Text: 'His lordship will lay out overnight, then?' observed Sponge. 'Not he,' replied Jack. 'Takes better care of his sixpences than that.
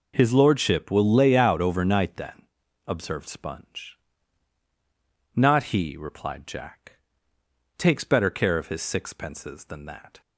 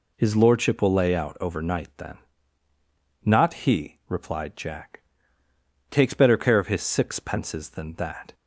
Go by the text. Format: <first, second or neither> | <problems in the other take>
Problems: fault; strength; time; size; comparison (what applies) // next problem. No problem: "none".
first | skips "observed Sponge"; at 2.7 s